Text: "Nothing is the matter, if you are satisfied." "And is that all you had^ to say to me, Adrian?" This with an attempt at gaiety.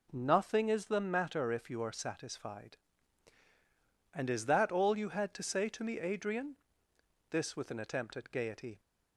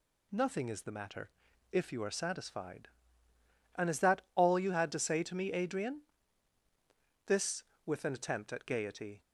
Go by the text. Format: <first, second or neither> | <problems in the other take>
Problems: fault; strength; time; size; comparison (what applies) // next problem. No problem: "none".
neither | none